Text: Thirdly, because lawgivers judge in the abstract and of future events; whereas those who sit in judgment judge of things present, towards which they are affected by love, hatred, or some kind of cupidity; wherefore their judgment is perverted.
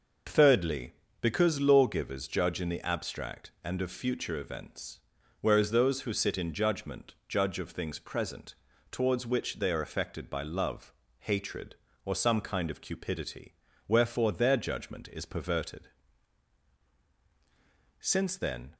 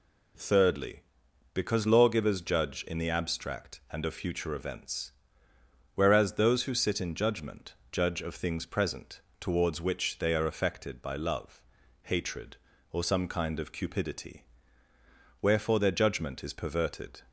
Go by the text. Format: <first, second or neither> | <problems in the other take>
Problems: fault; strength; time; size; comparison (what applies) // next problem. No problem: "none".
second | pauses between "judgment" and "judge"; slight; at 7.1 s; 0.16 s long; slight in the second // goes on to say "Since then"; noticeable; from 17.9 s on; 0.76 s long